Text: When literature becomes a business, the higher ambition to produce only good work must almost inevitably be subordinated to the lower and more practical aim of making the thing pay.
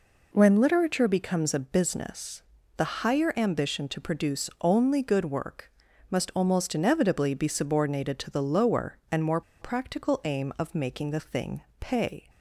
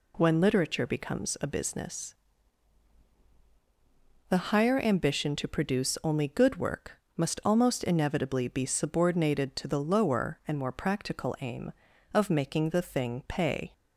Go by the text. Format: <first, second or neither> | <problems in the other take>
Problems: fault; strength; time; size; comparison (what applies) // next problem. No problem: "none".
second | pauses between "work" and "must"; at 5.6 s; 0.40 s long; slight in the second // pauses between "more" and "practical"; slight; at 9.4 s; 0.19 s long // pauses between "thing" and "pay"; slight; at 11.6 s; 0.18 s long